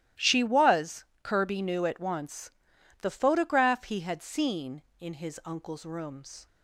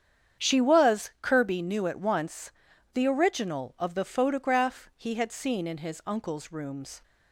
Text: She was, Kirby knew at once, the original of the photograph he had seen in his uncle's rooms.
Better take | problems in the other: second | starts louder than the rest; strong; until 1.3 s; 14 dB; strong in the second // skips "original of the"; at 3.0 s

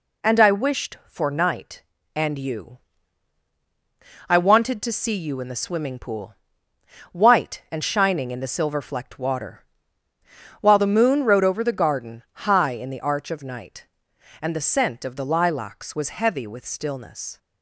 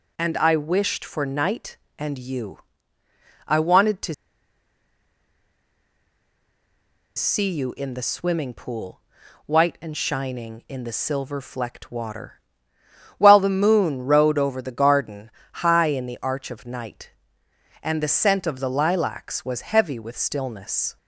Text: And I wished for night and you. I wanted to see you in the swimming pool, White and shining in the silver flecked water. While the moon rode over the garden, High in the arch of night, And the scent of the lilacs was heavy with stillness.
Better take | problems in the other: first | pauses between "to" and "see"; strong; at 4.1 s; 3.0 s long

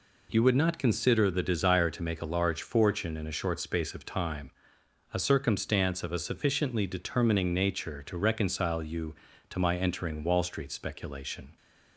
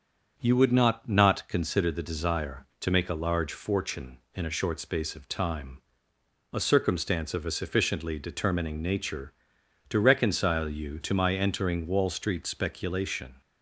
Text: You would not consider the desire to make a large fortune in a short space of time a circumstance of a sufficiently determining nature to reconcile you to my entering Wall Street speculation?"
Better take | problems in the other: first | starts louder than the rest; until 1.4 s; 7 dB // says "not" twice; at 1.0 s // pauses between "time" and "a"; noticeable; at 5.8 s; 0.72 s long; noticeable in the first

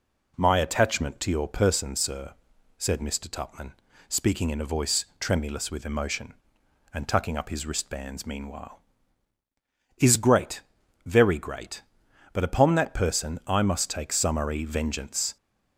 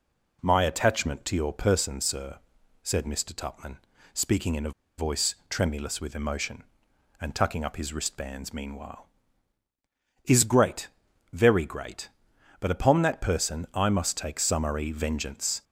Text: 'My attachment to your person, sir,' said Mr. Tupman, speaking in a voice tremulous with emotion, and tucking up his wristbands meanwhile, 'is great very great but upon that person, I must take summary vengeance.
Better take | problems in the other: first | pauses between "a" and "voice"; slight; at 4.7 s; 0.27 s long // pauses between "great" and "very"; noticeable; at 10.8 s; 0.46 s long; noticeable in the first

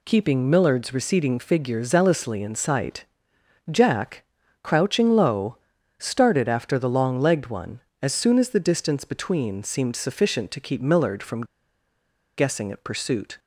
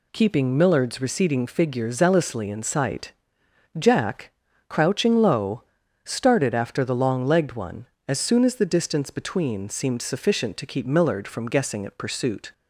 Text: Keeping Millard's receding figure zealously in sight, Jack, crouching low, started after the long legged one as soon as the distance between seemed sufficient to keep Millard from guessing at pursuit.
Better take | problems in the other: second | pauses between "from" and "guessing"; noticeable; at 11.4 s; 0.93 s long

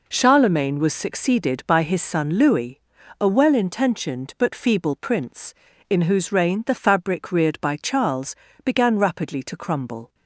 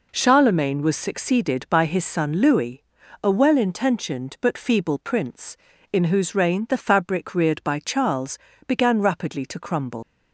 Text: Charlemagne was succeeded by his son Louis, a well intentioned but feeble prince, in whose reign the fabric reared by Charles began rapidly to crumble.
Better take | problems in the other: first | pauses between "Charles" and "began"; slight; at 8.3 s; 0.30 s long; slight in the first // leaves "crumble" unfinished; at 10.0 s; 140 ms

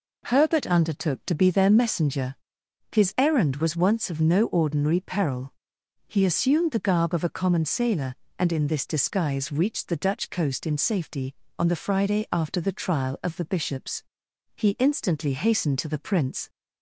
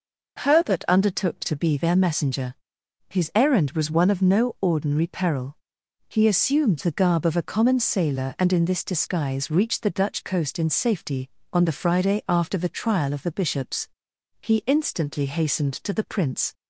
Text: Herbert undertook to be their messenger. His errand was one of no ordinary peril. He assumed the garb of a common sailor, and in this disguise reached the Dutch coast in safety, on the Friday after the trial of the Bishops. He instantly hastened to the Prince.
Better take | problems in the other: second | says "once" for "one"; at 3.7 s

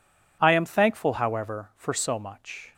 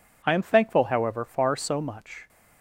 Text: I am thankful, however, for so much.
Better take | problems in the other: first | says "far" for "for"; at 1.2 s

